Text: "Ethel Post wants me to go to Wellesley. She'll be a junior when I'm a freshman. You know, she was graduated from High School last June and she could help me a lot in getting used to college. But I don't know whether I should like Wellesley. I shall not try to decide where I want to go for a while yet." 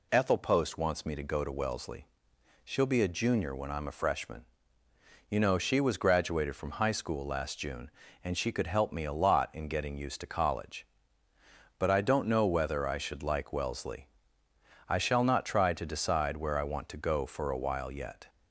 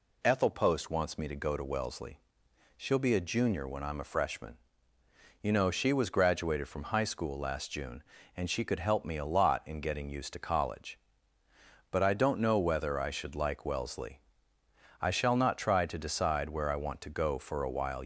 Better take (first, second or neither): first